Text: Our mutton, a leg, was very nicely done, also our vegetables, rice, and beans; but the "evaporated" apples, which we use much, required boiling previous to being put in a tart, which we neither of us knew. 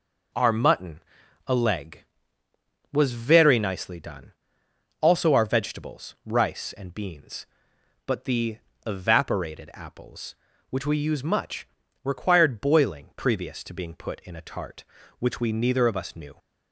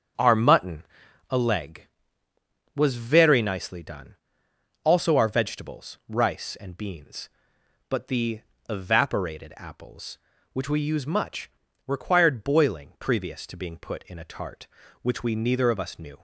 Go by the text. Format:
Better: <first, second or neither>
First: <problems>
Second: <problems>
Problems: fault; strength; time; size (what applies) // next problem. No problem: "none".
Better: first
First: pauses between "the" and "evaporated"; slight; at 8.5 s; 0.30 s long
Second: starts louder than the rest; strong; until 1.3 s; 7.5 dB // pauses between "the" and "evaporated"; slight; at 8.3 s; 0.30 s long